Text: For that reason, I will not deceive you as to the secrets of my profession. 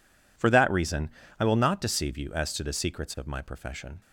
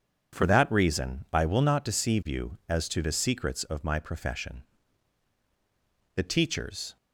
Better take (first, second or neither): first